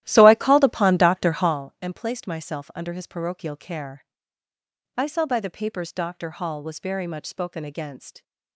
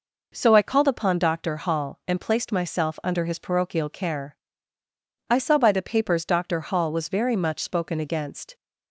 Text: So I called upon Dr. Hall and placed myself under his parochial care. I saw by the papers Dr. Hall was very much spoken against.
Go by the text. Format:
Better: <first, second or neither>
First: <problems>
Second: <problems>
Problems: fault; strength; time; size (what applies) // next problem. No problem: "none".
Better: second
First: starts louder than the rest; strong; until 1.6 s; 13.5 dB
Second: none